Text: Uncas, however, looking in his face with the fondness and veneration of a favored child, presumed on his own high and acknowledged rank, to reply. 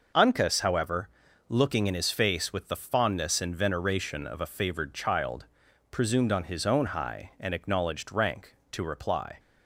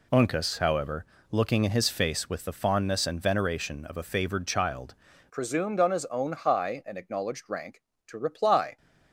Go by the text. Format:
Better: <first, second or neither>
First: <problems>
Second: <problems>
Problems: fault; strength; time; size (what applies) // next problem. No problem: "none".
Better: first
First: none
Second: changes voice at "presumed"; from 5.2 s on; 3.5 s long